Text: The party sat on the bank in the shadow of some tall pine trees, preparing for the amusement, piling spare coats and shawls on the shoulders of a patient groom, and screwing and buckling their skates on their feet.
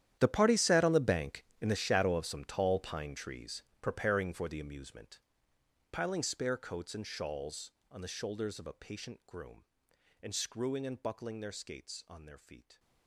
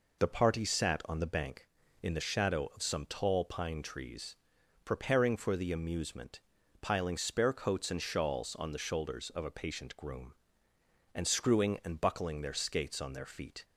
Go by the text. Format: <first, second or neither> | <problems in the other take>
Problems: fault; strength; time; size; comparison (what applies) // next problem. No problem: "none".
second | gets quieter; strong; throughout; 18 dB